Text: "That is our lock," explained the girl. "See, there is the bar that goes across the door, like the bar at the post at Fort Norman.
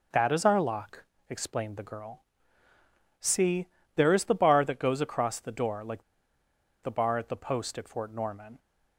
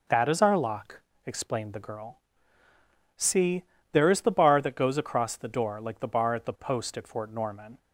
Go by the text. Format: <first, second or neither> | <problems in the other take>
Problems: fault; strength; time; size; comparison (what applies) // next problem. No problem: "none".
second | pauses between "like" and "the"; noticeable; at 6.0 s; 0.80 s long